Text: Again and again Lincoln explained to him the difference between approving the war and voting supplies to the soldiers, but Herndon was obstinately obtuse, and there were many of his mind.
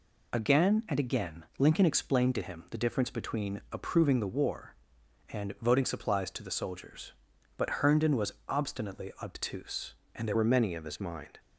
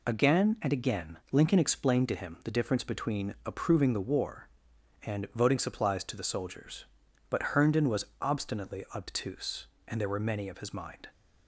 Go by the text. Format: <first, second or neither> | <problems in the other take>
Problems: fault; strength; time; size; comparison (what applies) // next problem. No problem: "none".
second | changes voice at "were"; from 10.3 s on; 1.0 s long